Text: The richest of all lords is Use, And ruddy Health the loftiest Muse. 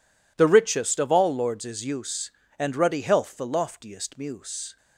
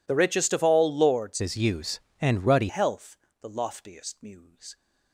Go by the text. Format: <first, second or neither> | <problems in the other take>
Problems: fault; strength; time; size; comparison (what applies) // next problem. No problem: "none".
first | changes voice from "is" to "ruddy"; from 1.3 to 2.6 s; 1.3 s long // pauses between "Health" and "the"; slight; at 3.1 s; 0.24 s long